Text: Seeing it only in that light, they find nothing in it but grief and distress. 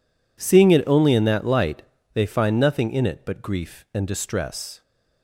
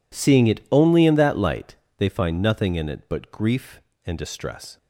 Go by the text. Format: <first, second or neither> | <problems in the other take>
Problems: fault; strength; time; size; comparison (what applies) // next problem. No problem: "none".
neither | none